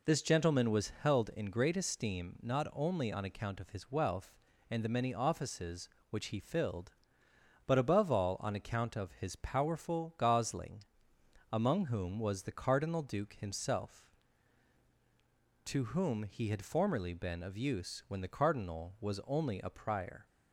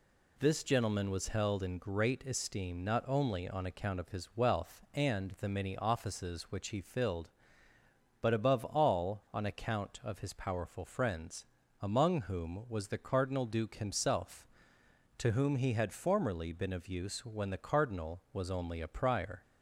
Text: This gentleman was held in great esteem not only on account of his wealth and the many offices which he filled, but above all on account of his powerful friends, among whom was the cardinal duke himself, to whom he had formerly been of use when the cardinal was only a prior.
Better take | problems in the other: second | says "gosling" for "friends"; at 10.1 s

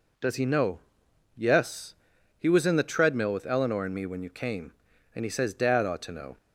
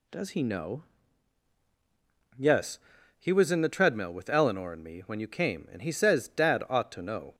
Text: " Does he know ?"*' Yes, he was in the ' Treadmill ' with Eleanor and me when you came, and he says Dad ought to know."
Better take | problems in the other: neither | none

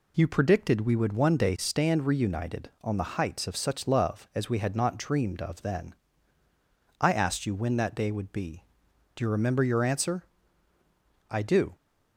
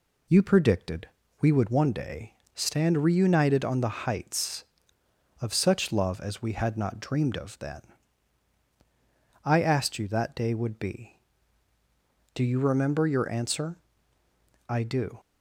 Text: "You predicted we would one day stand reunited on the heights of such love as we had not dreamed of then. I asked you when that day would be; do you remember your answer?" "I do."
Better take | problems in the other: first | pauses between "predicted" and "we"; slight; at 1.0 s; 0.32 s long // pauses between "day" and "stand"; slight; at 2.3 s; 0.22 s long // skips "when"; at 10.0 s

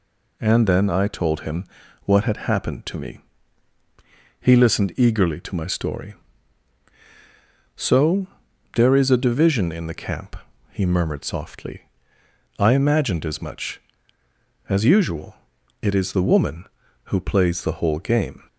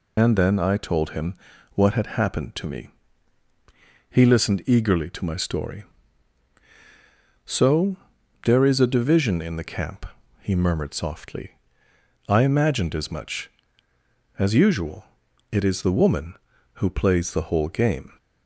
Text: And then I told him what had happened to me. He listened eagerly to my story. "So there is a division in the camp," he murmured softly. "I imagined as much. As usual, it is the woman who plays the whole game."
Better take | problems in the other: first | loses the start of "And"; at 0.1 s; 85 ms // pauses between "him" and "what"; at 1.3 s; 0.38 s long; also in the first // pauses between "So" and "there"; noticeable; at 7.9 s; 0.48 s long; noticeable in the first

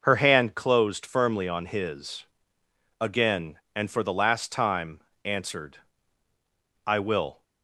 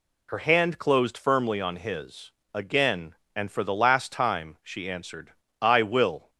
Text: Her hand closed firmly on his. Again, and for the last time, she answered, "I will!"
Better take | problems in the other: second | skips "she"; at 5.1 s

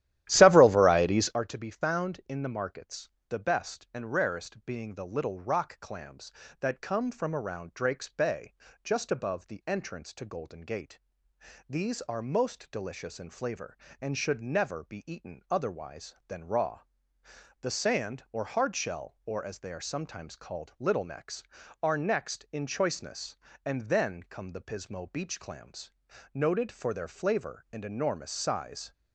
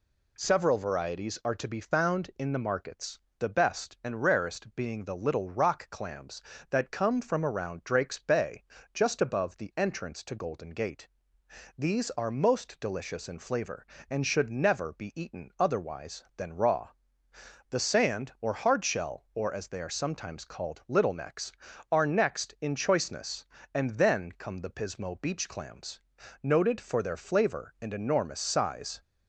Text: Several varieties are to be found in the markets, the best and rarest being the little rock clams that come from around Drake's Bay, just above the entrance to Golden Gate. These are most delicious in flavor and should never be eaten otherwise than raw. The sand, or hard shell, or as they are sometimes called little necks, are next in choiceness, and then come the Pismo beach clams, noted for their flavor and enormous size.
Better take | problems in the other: second | starts louder than the rest; strong; until 1.4 s; 13.5 dB

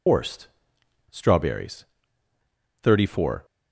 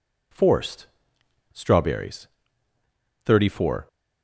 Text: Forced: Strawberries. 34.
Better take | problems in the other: second | loses the start of "Forced"; at 0.0 s; 130 ms

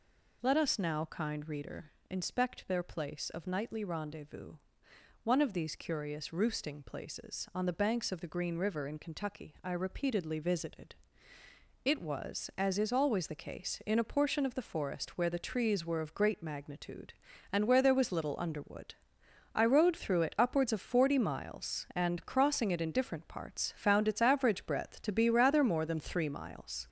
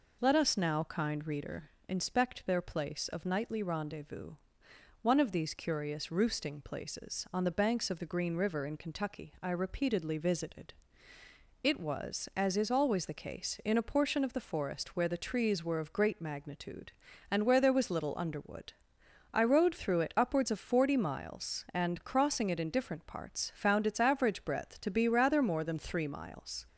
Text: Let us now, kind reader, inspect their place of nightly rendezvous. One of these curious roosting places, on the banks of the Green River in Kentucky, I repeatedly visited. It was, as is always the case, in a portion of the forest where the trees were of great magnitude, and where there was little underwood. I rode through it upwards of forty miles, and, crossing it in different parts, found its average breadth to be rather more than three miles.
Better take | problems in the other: second | gets louder; noticeable; throughout; 4.5 dB

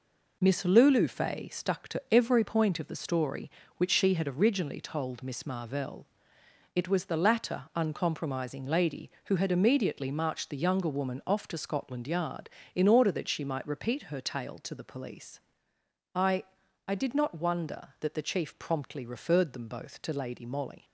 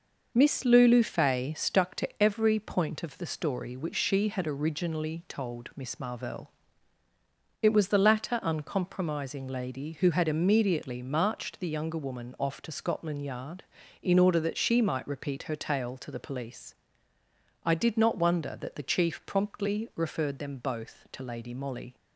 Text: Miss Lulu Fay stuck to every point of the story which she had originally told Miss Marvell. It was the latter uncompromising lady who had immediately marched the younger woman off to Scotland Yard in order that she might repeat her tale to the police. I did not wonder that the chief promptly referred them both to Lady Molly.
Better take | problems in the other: second | says "I" twice; at 16.8 s

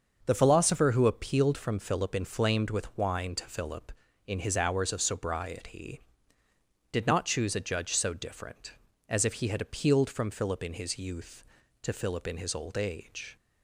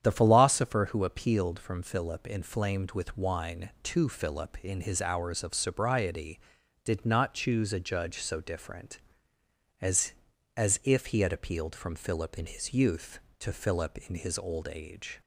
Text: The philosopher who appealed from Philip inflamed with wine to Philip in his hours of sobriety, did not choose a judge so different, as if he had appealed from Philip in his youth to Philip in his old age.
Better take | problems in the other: first | starts louder than the rest; strong; until 1.0 s; 9 dB; also in the first // says "as" twice; at 10.5 s

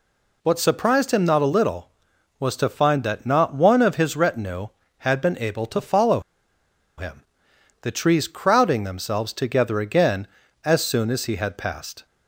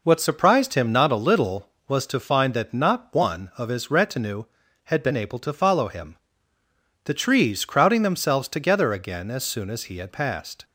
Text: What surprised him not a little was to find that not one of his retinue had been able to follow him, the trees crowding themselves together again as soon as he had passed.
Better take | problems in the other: second | pauses between "follow" and "him"; noticeable; at 6.1 s; 0.77 s long

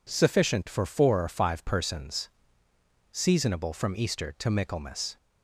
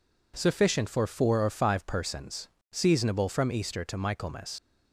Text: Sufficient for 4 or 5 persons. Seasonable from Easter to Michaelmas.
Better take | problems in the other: first | leaves "Michaelmas" unfinished; at 4.5 s; 70 ms

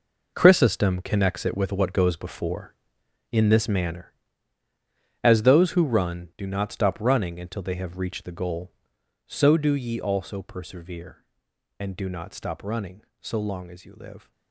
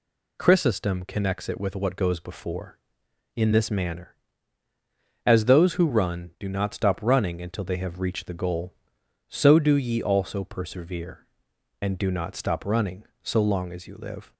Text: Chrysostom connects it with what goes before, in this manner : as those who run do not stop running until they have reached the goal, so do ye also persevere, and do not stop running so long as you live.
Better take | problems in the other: second | gets quieter; strong; throughout; 12 dB

